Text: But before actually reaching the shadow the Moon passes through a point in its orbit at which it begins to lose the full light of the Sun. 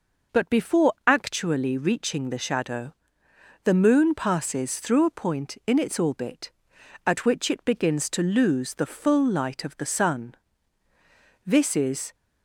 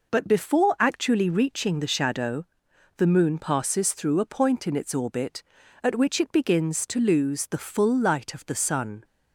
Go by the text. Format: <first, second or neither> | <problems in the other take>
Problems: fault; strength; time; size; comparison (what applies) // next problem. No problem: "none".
second | pauses between "shadow" and "the"; noticeable; at 2.9 s; 0.70 s long; noticeable in the second // goes on to say "This is"; noticeable; from 11.4 s on; 0.68 s long